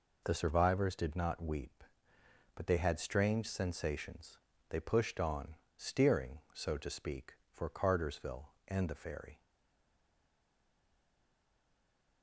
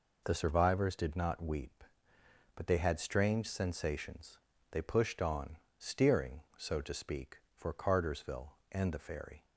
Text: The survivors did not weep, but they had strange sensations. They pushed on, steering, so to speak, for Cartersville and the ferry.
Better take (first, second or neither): second